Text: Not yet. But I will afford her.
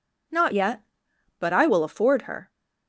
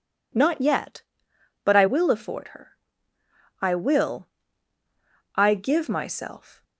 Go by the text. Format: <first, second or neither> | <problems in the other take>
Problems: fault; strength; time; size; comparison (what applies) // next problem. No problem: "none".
first | goes on to say "I will I give myself"; strong; from 3.6 s on; 3.0 s long